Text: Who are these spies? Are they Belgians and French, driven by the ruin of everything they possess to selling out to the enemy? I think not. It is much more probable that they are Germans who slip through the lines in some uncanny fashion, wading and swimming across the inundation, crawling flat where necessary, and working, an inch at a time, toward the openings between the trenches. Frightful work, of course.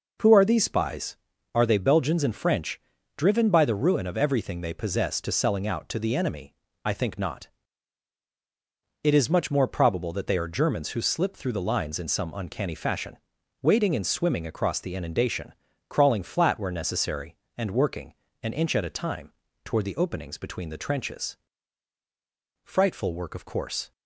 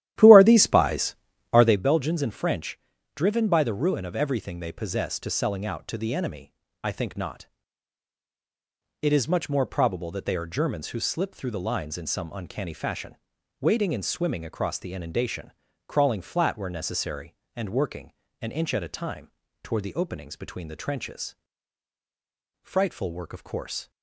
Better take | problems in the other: first | starts louder than the rest; strong; until 1.8 s; 12.5 dB

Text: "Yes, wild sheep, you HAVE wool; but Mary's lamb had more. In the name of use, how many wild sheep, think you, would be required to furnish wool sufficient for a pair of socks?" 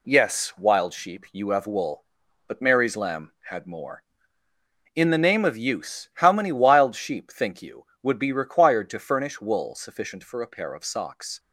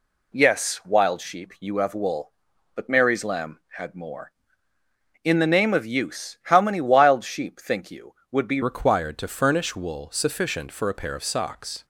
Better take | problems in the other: first | changes voice at "required"; from 8.6 s on; 3.2 s long

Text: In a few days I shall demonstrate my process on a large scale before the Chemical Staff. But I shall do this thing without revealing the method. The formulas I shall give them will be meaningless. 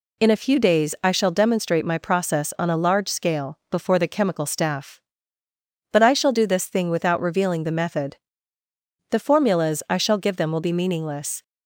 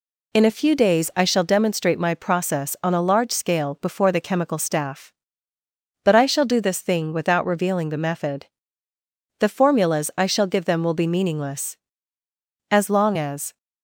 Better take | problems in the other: first | goes on to say "As long as"; noticeable; from 12.6 s on; 0.87 s long

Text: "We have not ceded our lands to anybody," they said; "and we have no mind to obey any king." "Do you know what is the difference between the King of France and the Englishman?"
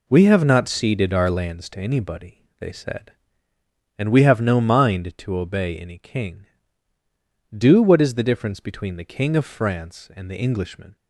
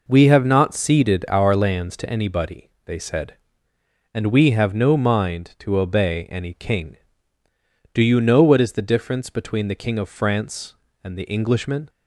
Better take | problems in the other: second | skips "you know"; at 7.8 s

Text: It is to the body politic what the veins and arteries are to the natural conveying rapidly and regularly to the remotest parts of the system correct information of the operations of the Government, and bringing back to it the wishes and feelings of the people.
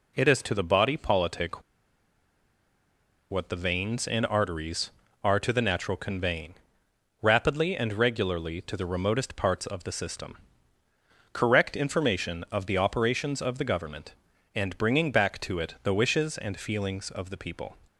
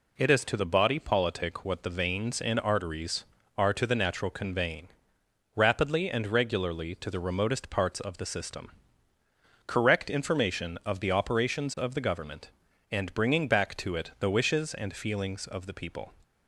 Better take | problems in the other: second | pauses between "politic" and "what"; strong; at 1.6 s; 1.7 s long // pauses between "conveying" and "rapidly"; noticeable; at 6.5 s; 0.68 s long; noticeable in the second // pauses between "system" and "correct"; noticeable; at 10.3 s; 0.94 s long; noticeable in the second

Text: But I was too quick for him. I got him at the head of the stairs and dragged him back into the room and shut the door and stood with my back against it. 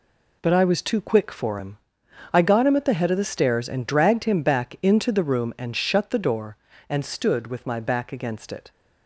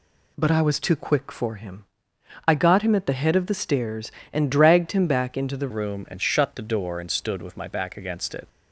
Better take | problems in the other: first | changes voice at "room"; from 5.7 s on; 2.7 s long

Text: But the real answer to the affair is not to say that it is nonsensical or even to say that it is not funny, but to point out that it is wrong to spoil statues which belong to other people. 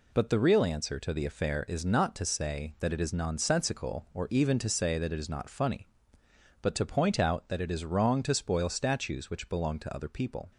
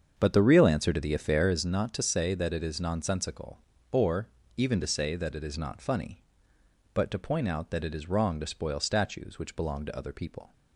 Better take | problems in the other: first | starts louder than the rest; strong; until 1.6 s; 7 dB // pauses between "or" and "even"; slight; at 4.2 s; 0.28 s long

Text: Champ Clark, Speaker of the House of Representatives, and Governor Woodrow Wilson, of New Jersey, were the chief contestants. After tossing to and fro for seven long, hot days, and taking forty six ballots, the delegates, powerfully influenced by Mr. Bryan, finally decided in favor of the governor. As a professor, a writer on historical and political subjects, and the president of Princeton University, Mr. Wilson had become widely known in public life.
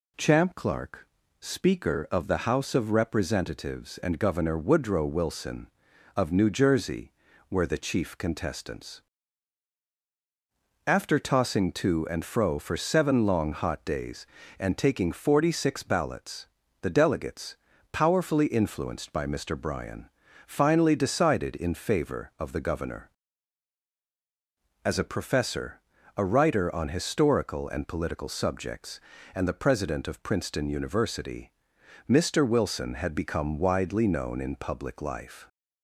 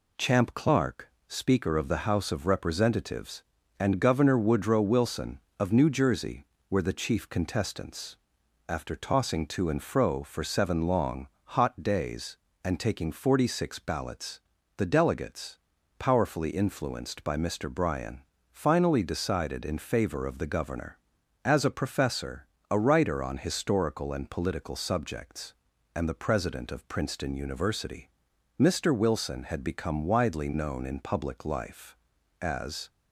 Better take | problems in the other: first | goes on to say "As"; slight; from 32.4 s on; 0.48 s long

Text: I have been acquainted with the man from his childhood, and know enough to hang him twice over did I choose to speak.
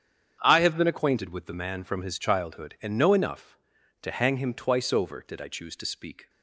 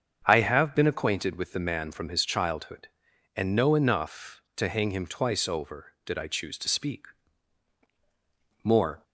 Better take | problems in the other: first | starts louder than the rest; strong; until 1.2 s; 7 dB; strong in the first // goes on to say "More"; slight; from 8.6 s on; 0.40 s long

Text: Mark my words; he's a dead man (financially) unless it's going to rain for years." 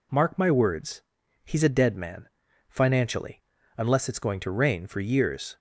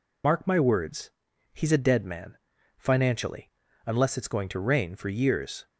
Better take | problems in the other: first | loses the start of "Mark"; at 0.2 s; 45 ms

